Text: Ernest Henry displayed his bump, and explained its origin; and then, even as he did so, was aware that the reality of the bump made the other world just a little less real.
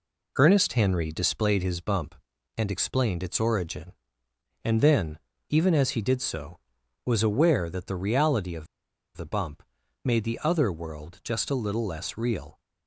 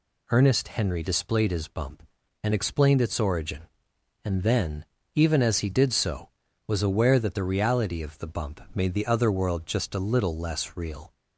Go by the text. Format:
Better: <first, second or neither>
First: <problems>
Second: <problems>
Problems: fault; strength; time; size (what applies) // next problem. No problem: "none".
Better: second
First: pauses between "of" and "the"; noticeable; at 8.6 s; 0.50 s long // pauses between "bump" and "made"; at 9.6 s; 0.44 s long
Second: none